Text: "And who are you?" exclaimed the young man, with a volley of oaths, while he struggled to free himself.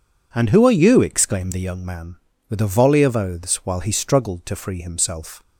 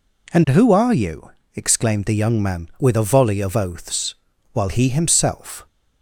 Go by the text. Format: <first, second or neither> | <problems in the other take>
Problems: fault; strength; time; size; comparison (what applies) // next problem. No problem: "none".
first | skips "struggled to free"; at 4.8 s